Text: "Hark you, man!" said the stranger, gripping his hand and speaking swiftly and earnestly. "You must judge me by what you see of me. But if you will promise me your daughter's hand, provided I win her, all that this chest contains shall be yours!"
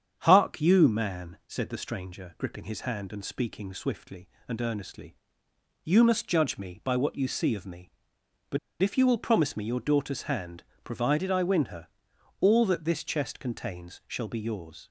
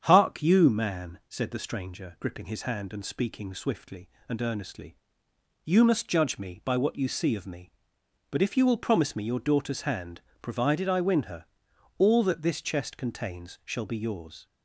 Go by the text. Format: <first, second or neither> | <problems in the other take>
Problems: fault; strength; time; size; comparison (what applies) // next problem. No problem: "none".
second | starts louder than the rest; strong; until 1.2 s; 8 dB; strong in the second // pauses between "But" and "if"; slight; at 8.5 s; 0.23 s long